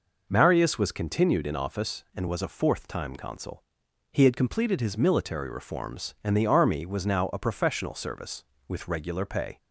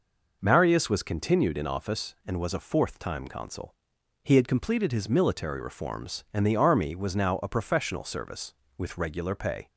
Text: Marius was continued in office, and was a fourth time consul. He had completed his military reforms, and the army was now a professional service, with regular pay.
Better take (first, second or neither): neither